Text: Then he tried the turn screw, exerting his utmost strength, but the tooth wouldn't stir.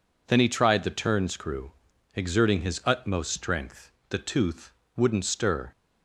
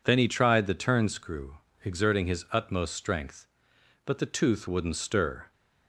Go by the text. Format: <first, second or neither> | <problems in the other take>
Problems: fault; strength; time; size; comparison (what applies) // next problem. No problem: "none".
second | skips "but"; at 4.0 s // pauses between "tooth" and "wouldn't"; slight; at 4.7 s; 0.24 s long